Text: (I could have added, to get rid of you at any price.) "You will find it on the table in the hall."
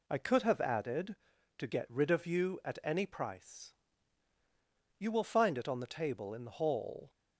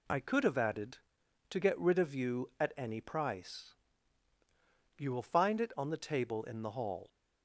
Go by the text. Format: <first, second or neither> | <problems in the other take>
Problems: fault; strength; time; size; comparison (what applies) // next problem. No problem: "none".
neither | none